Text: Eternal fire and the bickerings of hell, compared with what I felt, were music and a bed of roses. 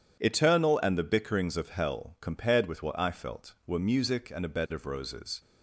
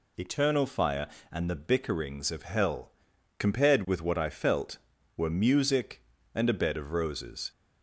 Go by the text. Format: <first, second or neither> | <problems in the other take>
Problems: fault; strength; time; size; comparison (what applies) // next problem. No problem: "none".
second | skips "fire"; at 0.8 s